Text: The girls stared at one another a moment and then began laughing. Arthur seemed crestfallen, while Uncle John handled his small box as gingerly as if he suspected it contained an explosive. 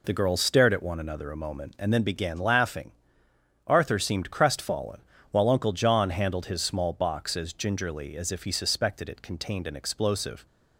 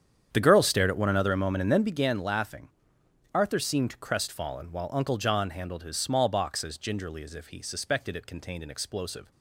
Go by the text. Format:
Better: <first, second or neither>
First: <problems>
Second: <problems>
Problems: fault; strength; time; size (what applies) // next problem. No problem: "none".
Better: first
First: none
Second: starts louder than the rest; strong; until 2.1 s; 8.5 dB